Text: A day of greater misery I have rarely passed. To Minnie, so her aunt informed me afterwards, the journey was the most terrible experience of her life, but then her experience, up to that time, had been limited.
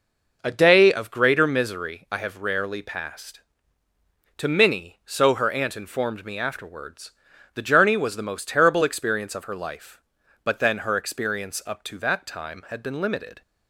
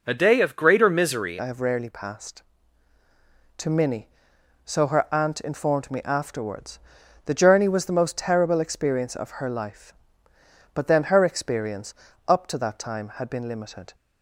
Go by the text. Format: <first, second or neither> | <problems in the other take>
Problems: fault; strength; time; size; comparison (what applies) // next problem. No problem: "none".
first | changes voice at "I"; from 1.3 s on; 12.6 s long